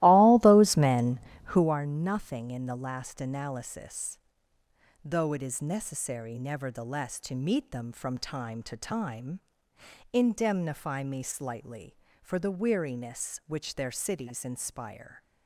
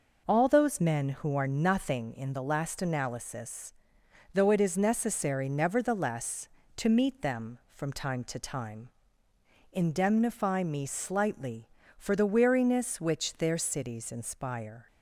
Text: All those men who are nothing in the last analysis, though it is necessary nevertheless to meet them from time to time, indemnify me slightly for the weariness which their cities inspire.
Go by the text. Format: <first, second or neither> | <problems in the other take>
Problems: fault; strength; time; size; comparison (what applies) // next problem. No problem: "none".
second | starts louder than the rest; strong; until 1.7 s; 16.5 dB